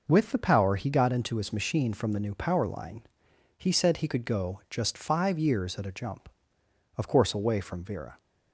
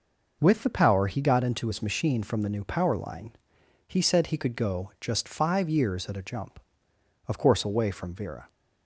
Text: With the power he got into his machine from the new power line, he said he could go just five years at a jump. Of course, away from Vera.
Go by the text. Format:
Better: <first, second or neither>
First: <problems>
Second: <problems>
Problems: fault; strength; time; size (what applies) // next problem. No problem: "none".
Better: neither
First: none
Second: none